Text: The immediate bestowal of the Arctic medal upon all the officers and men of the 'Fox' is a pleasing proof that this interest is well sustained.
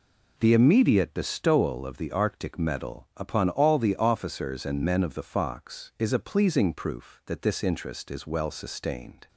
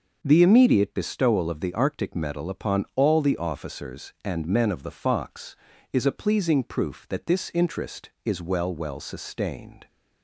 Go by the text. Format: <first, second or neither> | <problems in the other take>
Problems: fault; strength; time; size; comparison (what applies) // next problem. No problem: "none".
first | starts louder than the rest; noticeable; until 1.2 s; 6 dB // says "well" twice; at 8.7 s